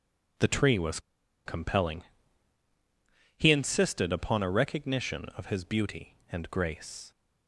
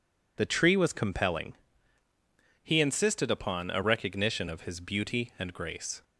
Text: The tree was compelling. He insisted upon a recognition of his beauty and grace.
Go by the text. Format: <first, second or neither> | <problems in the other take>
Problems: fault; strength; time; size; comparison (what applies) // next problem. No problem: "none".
second | pauses between "was" and "compelling"; noticeable; at 0.9 s; 0.46 s long